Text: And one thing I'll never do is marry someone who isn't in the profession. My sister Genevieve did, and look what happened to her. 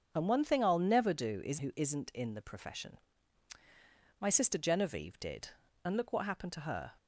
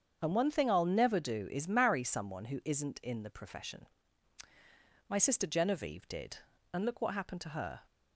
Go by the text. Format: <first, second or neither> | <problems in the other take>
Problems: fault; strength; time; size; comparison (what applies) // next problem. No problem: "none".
second | starts louder than the rest; until 1.1 s; 7 dB; strong in the second // skips "marry someone"; at 1.5 s